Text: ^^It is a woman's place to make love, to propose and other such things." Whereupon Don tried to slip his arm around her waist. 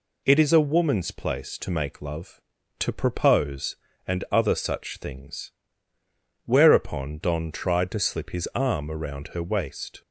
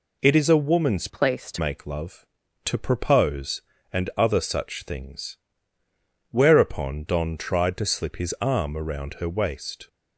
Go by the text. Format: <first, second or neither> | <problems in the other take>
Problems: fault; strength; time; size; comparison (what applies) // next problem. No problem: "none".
first | changes voice from "place" to "to"; from 1.0 to 1.5 s; 0.5 s long